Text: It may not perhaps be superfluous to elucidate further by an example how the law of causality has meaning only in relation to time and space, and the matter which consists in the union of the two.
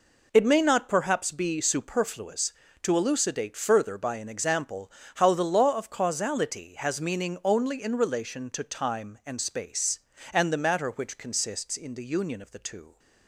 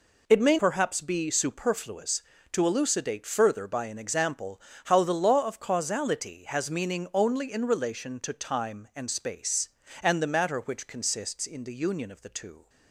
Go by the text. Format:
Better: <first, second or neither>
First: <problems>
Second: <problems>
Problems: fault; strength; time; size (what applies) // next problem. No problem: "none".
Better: first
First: pauses between "example" and "how"; slight; at 4.9 s; 0.24 s long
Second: skips "not"; at 0.5 s // pauses between "example" and "how"; slight; at 4.6 s; 0.24 s long